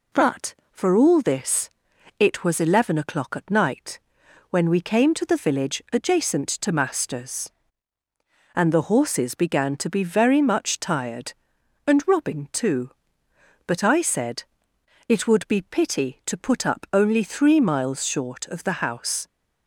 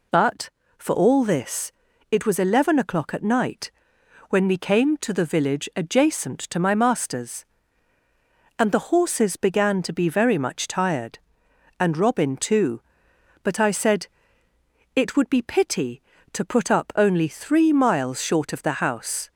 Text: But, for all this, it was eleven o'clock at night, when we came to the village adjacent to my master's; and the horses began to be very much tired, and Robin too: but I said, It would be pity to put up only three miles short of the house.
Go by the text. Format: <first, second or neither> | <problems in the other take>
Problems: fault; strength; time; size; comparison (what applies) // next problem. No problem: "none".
second | skips "my"; at 6.7 s